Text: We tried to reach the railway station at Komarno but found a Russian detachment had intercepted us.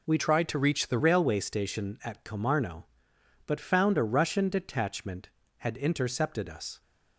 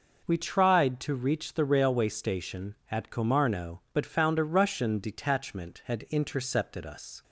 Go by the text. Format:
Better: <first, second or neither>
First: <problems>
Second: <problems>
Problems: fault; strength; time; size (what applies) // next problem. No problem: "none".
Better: second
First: changes voice from "tried" to "the"; from 0.1 to 0.9 s; 0.8 s long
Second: none